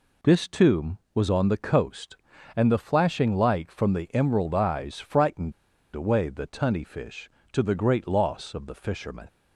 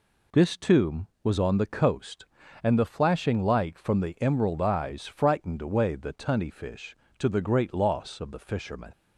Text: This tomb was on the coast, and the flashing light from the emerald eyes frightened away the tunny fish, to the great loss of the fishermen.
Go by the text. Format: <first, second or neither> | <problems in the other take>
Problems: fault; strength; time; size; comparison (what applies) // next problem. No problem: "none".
second | pauses between "frightened" and "away"; at 5.5 s; 0.43 s long